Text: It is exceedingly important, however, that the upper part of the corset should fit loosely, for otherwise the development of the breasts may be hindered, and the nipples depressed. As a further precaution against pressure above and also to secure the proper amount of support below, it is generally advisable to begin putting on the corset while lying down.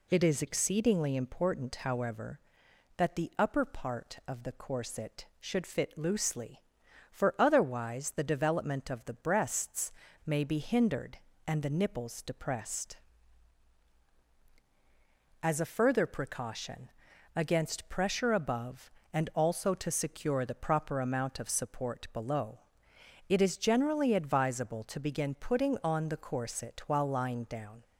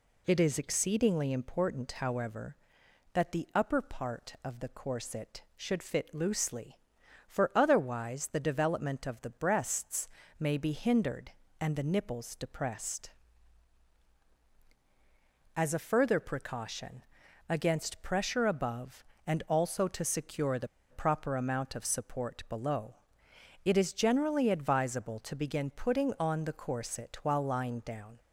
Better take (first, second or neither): first